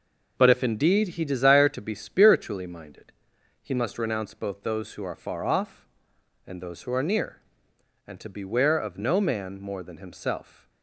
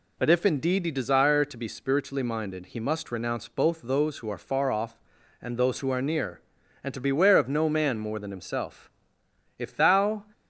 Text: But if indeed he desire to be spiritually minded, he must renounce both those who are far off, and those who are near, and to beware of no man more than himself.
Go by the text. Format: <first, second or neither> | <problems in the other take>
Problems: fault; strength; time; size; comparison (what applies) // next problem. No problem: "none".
first | goes on to say "If thou"; noticeable; from 9.5 s on; 0.64 s long